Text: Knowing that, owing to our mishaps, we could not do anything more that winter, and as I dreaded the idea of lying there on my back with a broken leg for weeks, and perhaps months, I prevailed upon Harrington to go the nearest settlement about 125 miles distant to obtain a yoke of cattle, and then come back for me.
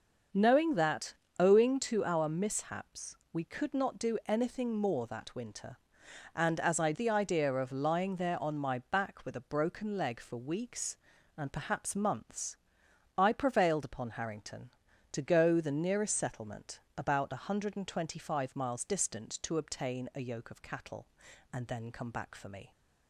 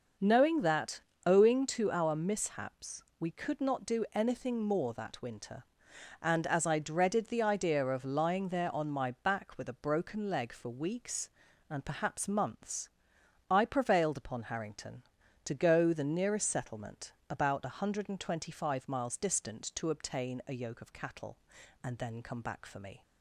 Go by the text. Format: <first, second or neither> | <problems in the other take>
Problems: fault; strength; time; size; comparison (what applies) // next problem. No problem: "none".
second | starts louder than the rest; noticeable; until 1.5 s; 6 dB // skips "dreaded"; at 6.9 s // pauses between "settlement" and "about"; slight; at 16.7 s; 0.18 s long; slight in the second